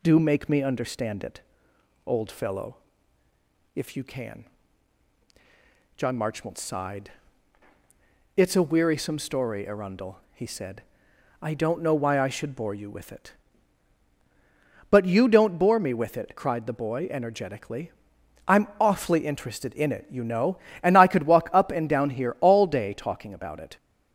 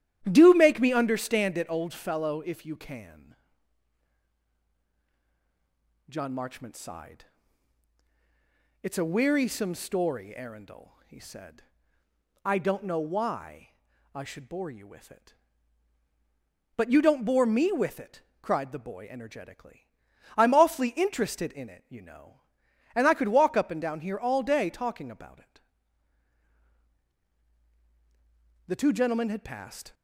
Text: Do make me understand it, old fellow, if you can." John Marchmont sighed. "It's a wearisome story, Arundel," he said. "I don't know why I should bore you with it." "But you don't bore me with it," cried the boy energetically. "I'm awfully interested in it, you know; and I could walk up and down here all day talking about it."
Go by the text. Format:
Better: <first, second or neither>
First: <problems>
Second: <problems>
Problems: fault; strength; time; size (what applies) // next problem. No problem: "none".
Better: first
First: none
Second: starts louder than the rest; strong; until 1.3 s; 11 dB // pauses between "why" and "I"; at 13.7 s; 0.44 s long // goes on to say "The two gentlemen had passed"; noticeable; from 28.6 s on; 1.2 s long